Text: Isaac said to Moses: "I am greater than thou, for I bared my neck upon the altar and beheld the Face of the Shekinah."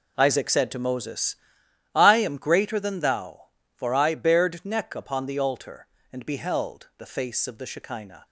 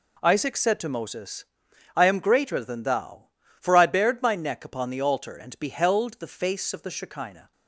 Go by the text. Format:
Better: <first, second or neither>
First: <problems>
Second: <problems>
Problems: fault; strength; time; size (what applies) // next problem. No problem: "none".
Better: second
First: skips "my"; at 4.6 s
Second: none